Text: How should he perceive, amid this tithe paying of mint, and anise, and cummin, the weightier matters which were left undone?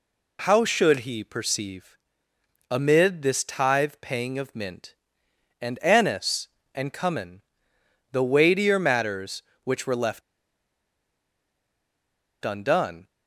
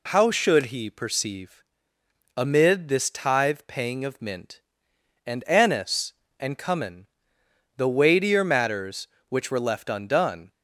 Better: second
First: pauses between "left" and "undone"; strong; at 10.2 s; 2.2 s long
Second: none

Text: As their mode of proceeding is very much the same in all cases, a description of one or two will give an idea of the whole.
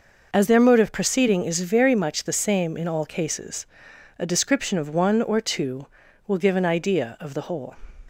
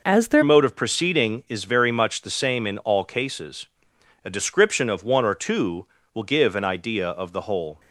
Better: first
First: none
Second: changes voice at "mode"; from 0.4 s on; 7.3 s long

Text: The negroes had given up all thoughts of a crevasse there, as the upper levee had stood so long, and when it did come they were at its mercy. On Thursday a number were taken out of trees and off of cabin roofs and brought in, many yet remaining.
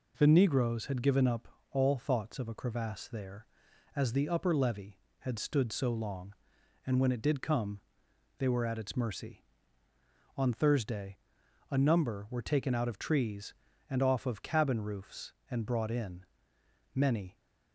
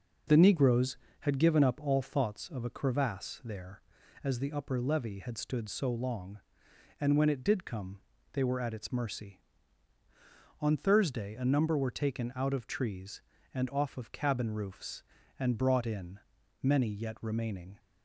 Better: second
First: pauses between "up" and "all"; slight; at 1.4 s; 0.24 s long // pauses between "come" and "they"; noticeable; at 7.7 s; 0.58 s long // pauses between "Thursday" and "a"; noticeable; at 11.1 s; 0.52 s long // stops before "yet remaining"; at 17.3 s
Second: pauses between "come" and "they"; slight; at 8.0 s; 0.32 s long

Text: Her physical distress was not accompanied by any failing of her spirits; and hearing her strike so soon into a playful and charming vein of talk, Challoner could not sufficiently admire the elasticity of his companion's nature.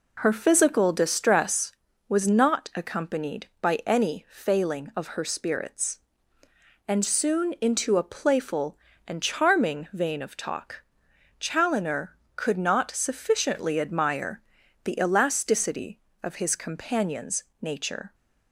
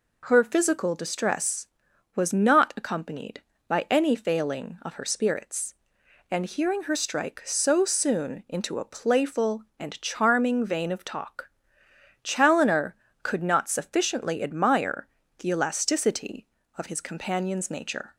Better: second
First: skips "hearing her strike so"; at 7.0 s // pauses between "admire" and "the"; at 14.3 s; 0.44 s long // pauses between "companion's" and "nature"; slight; at 17.4 s; 0.16 s long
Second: pauses between "admire" and "the"; slight; at 15.0 s; 0.30 s long

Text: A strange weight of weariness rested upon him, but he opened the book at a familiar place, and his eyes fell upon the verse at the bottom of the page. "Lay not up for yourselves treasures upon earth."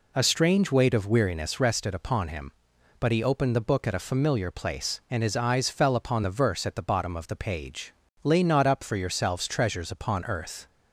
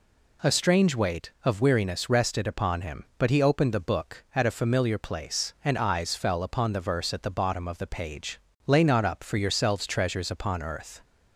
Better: first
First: none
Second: skips "his"; at 5.7 s

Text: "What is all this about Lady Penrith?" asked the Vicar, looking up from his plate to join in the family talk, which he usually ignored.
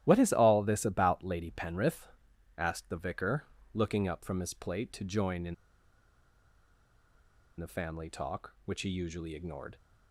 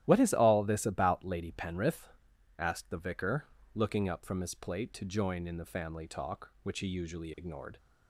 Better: second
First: starts louder than the rest; strong; until 1.0 s; 13 dB // pauses between "in" and "the"; strong; at 5.5 s; 2.0 s long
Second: starts louder than the rest; strong; until 1.0 s; 13 dB

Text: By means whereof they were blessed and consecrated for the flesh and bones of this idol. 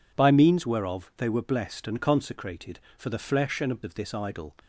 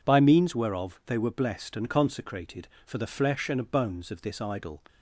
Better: second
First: skips "bones"; at 3.8 s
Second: none

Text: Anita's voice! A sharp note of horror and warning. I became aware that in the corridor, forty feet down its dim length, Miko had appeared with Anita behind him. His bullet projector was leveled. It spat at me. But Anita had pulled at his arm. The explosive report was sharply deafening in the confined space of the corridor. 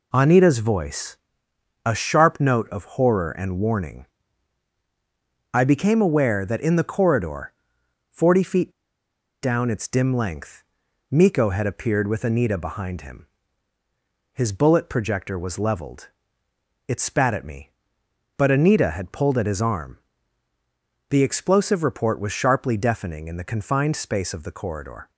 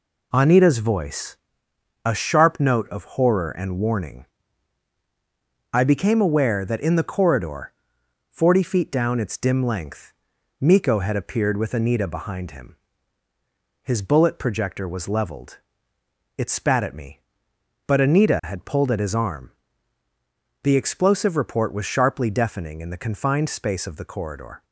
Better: second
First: pauses between "feet" and "down"; noticeable; at 8.7 s; 0.71 s long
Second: none

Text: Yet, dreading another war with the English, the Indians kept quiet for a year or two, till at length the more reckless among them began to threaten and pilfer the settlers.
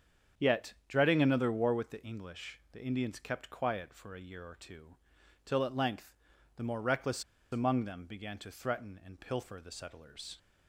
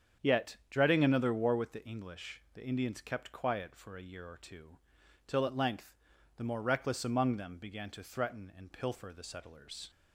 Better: second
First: starts louder than the rest; strong; until 1.5 s; 7.5 dB // pauses between "length" and "the"; at 6.1 s; 0.44 s long // pauses between "reckless" and "among"; slight; at 7.2 s; 0.28 s long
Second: starts louder than the rest; strong; until 1.3 s; 7.5 dB // pauses between "length" and "the"; at 5.9 s; 0.44 s long

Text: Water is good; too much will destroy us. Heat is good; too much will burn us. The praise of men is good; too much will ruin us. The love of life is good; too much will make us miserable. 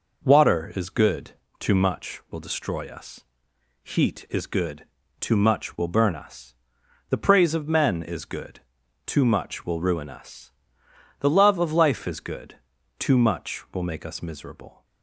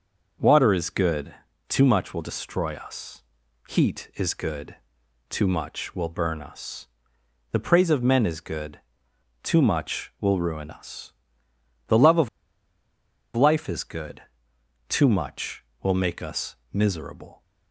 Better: first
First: none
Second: pauses between "of" and "life"; at 12.2 s; 1.0 s long // pauses between "us" and "miserable"; slight; at 16.5 s; 0.18 s long

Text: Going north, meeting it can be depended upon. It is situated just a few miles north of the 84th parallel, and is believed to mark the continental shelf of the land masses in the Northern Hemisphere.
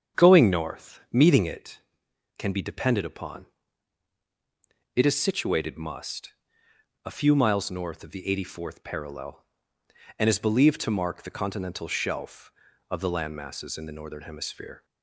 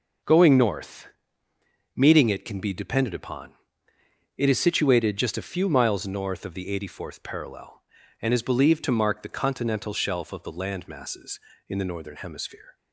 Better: second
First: starts louder than the rest; strong; until 1.2 s; 7.5 dB // says "must" for "just"; at 5.7 s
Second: none

